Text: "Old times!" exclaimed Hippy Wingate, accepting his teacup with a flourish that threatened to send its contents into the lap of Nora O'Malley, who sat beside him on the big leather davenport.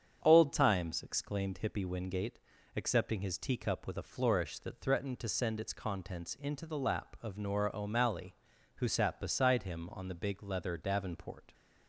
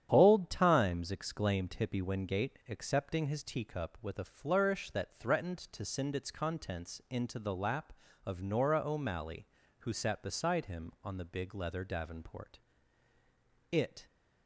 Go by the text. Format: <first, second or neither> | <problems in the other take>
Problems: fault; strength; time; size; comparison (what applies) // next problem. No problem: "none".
first | starts louder than the rest; strong; until 1.1 s; 10 dB; strong in the first // goes on to say "It"; slight; from 13.7 s on; 0.34 s long